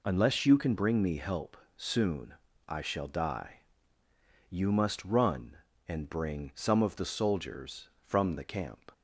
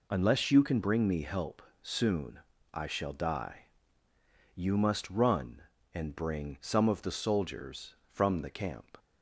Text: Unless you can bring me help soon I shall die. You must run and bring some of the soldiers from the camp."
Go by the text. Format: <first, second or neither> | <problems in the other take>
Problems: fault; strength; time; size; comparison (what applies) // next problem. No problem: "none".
neither | pauses between "help" and "soon"; slight; the same in both // pauses between "soon" and "I"; slight; the same in both